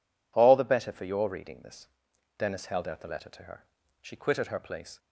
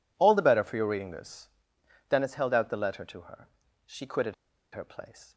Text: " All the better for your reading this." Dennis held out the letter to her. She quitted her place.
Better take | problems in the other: first | pauses between "quitted" and "her"; at 4.3 s; 0.40 s long

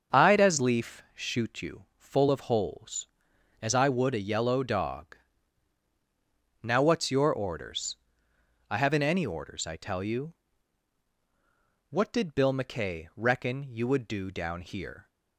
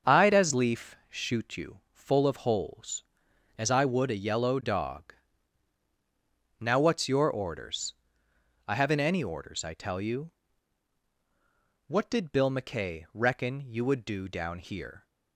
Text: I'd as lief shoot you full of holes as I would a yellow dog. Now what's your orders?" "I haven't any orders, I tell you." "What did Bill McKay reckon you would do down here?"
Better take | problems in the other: neither | starts louder than the rest; the same in both

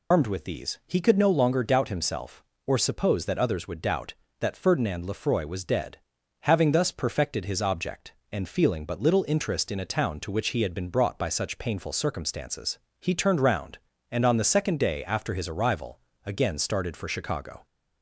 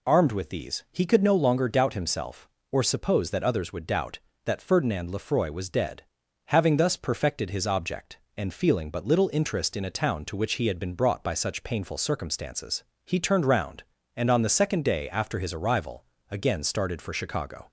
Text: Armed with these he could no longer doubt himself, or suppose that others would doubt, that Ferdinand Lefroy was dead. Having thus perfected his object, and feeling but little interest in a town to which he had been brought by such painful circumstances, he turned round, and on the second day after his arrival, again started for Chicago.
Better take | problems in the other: second | loses the start of "Armed"; at 0.1 s; 95 ms

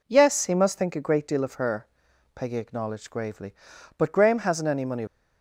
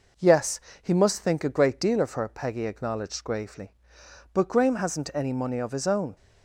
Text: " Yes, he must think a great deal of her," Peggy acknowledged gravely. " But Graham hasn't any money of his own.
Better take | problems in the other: second | stops before "of his own"; at 5.0 s

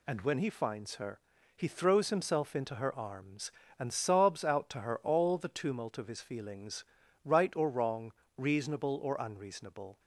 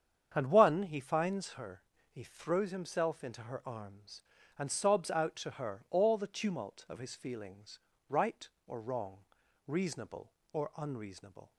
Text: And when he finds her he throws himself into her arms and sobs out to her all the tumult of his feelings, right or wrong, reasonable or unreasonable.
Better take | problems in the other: first | starts louder than the rest; strong; until 1.3 s; 8 dB // says "one" for "when"; at 0.5 s // pauses between "her" and "he"; slight; at 1.8 s; 0.30 s long; slight in the first

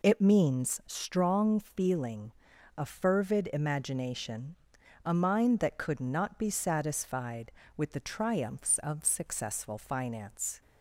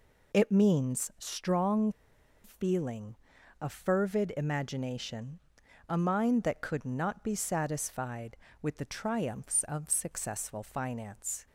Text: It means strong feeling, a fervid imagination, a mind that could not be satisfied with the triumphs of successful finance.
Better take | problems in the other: first | pauses between "strong" and "feeling"; noticeable; at 1.8 s; 0.54 s long

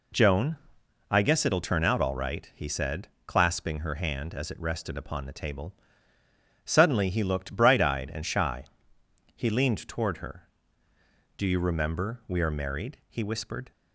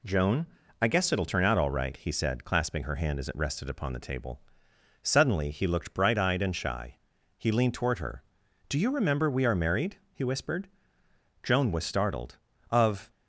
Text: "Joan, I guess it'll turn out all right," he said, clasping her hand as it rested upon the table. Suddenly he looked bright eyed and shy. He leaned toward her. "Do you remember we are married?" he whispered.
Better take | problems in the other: first | goes on to say "Joan was startled Of"; strong; from 11.4 s on; 1.6 s long

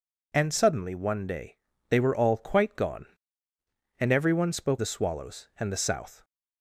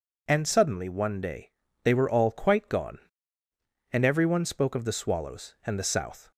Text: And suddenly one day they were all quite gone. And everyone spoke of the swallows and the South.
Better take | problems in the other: second | pauses between "day" and "they"; slight; at 1.5 s; 0.34 s long; slight in the second // skips "of"; at 4.7 s

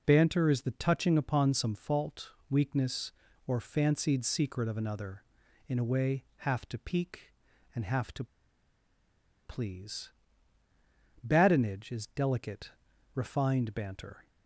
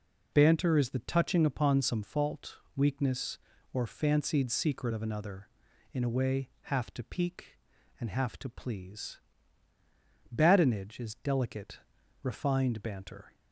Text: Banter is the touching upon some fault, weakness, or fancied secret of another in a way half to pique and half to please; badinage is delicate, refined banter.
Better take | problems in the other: second | pauses between "to" and "please"; at 8.2 s; 1.1 s long

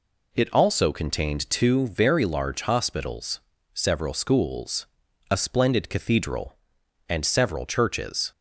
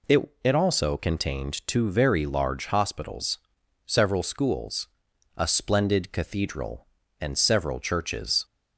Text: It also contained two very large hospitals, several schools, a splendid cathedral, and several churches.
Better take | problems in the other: first | says "It" twice; at 0.4 s

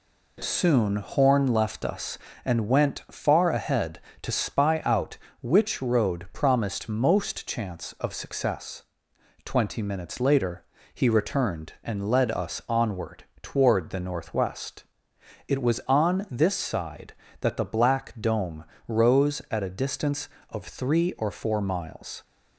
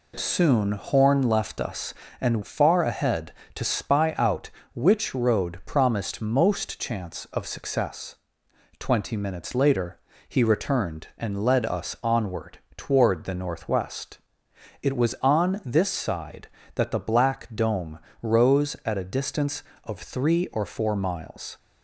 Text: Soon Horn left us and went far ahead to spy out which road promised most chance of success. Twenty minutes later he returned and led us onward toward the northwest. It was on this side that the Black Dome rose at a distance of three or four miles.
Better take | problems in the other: first | skips "went"; at 2.4 s // pauses between "later" and "he"; slight; at 9.9 s; 0.30 s long; slight in the first // pauses between "onward" and "toward"; slight; at 12.5 s; 0.18 s long; slight in the first // pauses between "Dome" and "rose"; slight; at 17.9 s; 0.24 s long; slight in the first

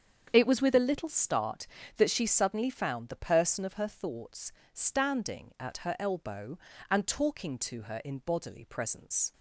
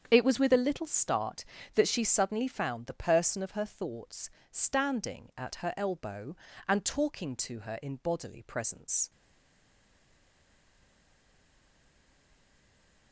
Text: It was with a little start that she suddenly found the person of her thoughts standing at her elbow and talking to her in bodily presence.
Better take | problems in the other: first | starts louder than the rest; strong; until 1.1 s; 7.5 dB; strong in the first // pauses between "thoughts" and "standing"; slight; at 4.2 s; 0.22 s long; slight in the first // stays silent after the last word; strong; from 9.0 s on; 4.1 s long

